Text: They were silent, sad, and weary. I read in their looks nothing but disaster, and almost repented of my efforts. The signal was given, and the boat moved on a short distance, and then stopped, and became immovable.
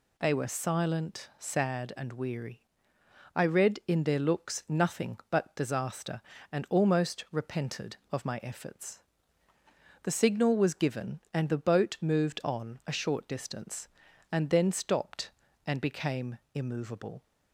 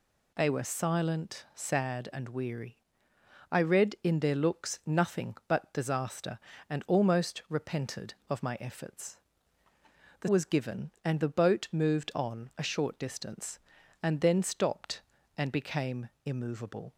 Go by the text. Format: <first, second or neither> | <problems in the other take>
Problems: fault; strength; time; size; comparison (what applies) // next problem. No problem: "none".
first | skips "signal"; at 10.2 s // pauses between "became" and "immovable"; slight; at 16.0 s; 0.16 s long; slight in the first